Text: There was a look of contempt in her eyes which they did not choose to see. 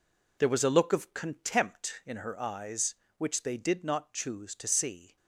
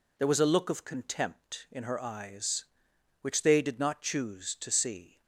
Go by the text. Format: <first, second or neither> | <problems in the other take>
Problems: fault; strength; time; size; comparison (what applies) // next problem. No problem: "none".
second | gets quieter; strong; throughout; 7.5 dB